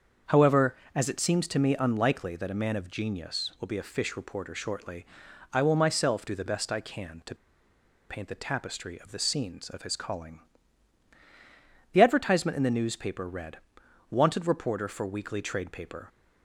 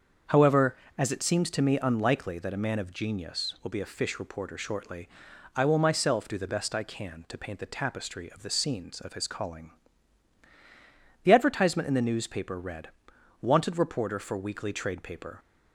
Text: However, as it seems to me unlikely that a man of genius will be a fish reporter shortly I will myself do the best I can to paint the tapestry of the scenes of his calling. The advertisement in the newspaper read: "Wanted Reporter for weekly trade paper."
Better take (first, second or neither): second